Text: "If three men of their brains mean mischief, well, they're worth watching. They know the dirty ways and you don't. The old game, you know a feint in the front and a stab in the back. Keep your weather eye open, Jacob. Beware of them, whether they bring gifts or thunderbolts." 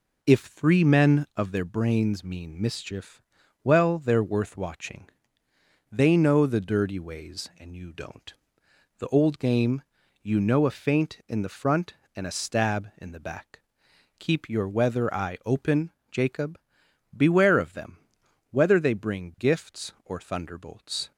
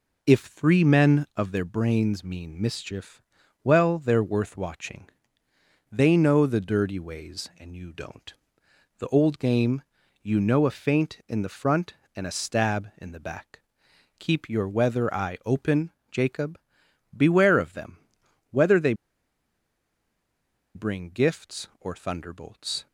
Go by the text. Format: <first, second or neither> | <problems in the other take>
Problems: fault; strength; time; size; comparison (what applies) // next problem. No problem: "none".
first | pauses between "they" and "bring"; strong; at 18.9 s; 1.8 s long